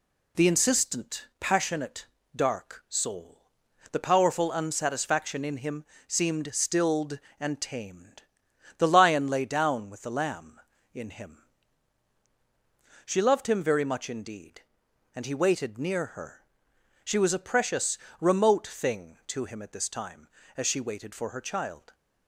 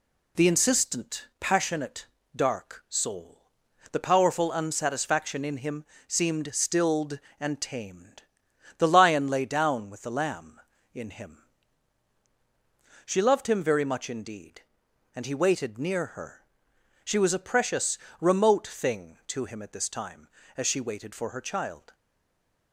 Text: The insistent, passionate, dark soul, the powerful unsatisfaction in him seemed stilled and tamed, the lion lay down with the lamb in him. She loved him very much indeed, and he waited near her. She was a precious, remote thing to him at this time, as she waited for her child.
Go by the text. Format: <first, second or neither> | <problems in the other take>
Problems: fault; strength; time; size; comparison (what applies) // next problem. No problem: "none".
first | pauses between "him" and "seemed"; slight; at 5.8 s; 0.22 s long; slight in the first // stays silent after the last word; slight; from 21.9 s on; 0.8 s long